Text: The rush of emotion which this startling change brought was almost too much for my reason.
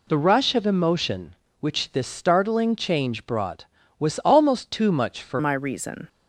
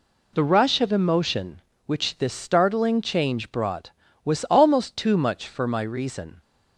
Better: second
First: changes voice at "my"; from 5.3 s on; 0.7 s long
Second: none

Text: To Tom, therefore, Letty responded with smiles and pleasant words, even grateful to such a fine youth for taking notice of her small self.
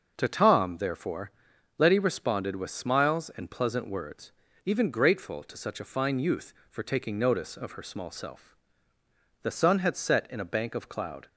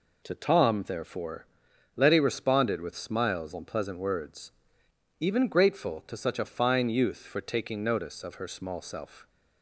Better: second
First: starts louder than the rest; noticeable; until 1.1 s; 6 dB // goes on to say "The sun had set in a bank of cloud"; strong; from 9.4 s on; 1.8 s long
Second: none

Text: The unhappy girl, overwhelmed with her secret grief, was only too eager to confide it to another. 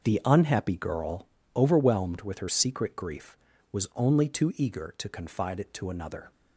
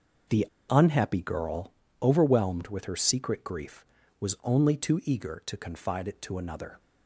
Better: first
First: starts louder than the rest; noticeable; until 1.0 s; 6 dB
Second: starts louder than the rest; noticeable; until 1.5 s; 6 dB // pauses between "The" and "unhappy"; slight; at 0.4 s; 0.23 s long

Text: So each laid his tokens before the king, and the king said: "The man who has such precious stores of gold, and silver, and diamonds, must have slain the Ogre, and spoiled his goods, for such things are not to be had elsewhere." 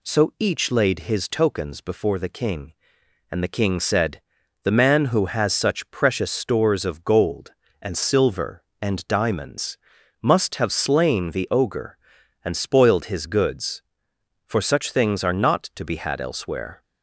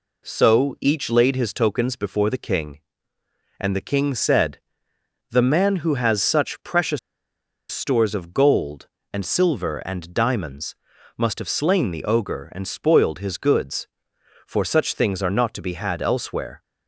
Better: first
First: none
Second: pauses between "precious" and "stores"; noticeable; at 6.9 s; 0.72 s long

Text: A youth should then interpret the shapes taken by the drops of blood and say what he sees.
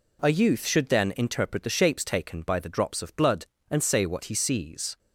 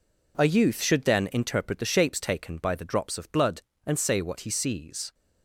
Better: first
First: none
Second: gets quieter; strong; throughout; 9.5 dB

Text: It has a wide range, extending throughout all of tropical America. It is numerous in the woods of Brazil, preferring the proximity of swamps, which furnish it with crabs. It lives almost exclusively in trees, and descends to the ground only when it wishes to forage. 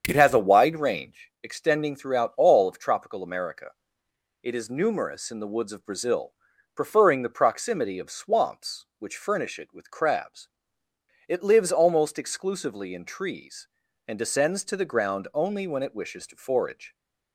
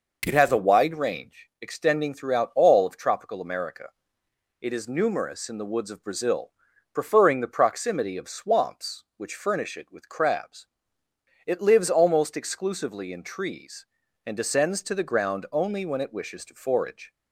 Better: second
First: starts louder than the rest; strong; until 1.3 s; 7.5 dB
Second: none

